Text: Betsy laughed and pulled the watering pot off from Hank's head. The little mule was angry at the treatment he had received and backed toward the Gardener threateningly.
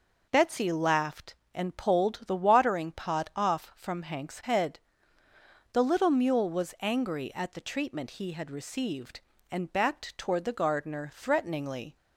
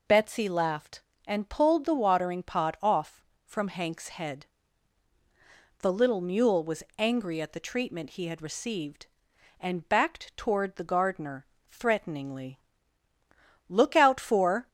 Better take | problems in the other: first | pauses between "Gardener" and "threateningly"; slight; at 11.4 s; 0.28 s long // goes on to say "Look out for"; noticeable; from 13.6 s on; 1.0 s long

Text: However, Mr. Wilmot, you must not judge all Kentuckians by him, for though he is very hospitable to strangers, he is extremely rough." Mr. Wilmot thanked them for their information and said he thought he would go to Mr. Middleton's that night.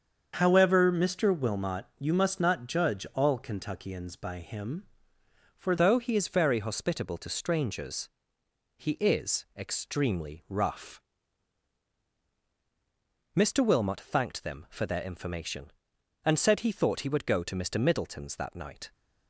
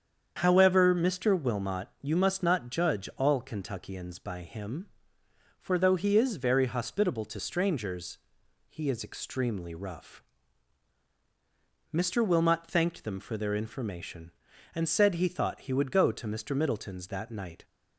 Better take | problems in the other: second | starts louder than the rest; until 1.3 s; 7 dB; strong in the second // changes voice at "though"; from 5.7 s on; 13.2 s long

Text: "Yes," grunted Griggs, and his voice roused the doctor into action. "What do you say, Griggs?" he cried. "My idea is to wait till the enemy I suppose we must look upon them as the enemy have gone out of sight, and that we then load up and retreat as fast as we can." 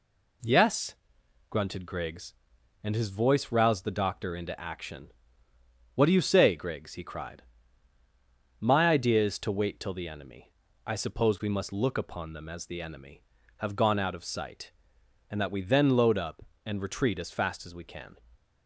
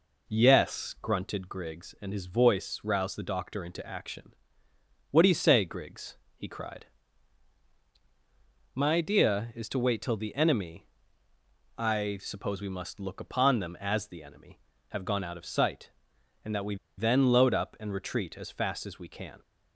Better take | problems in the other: first | pauses between "enemy" and "I"; noticeable; at 10.8 s; 0.94 s long; slight in the first // pauses between "we" and "then"; slight; at 16.7 s; 0.22 s long

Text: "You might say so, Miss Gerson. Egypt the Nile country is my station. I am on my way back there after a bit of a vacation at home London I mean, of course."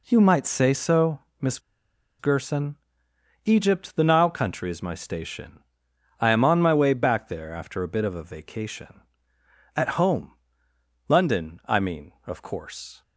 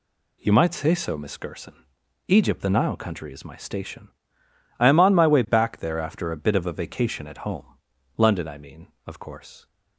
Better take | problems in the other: second | pauses between "Miss" and "Gerson"; noticeable; at 1.5 s; 0.60 s long // pauses between "home" and "London"; noticeable; at 10.3 s; 0.74 s long; noticeable in the second

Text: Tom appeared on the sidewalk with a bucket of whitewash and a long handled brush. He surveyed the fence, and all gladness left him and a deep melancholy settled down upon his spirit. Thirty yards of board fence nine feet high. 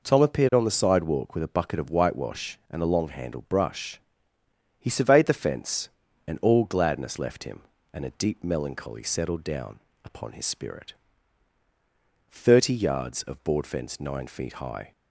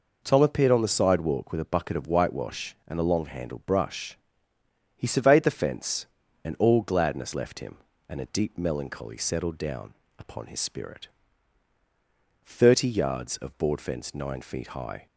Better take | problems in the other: neither | pauses between "down" and "upon"; slight; the same in both

